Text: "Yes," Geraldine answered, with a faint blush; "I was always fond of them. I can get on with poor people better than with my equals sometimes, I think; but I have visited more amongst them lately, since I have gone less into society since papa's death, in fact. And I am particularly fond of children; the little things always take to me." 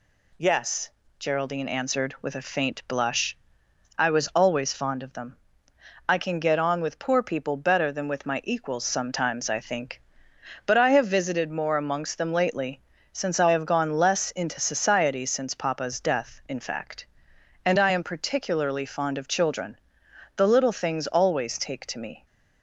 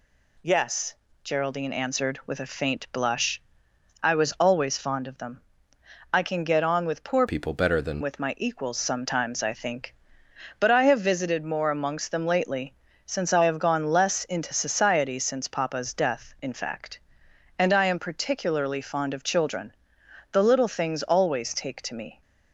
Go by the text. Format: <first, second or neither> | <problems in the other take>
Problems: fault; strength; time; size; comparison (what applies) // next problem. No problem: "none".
first | changes voice from "people" to "than"; from 7.2 to 8.0 s; 0.8 s long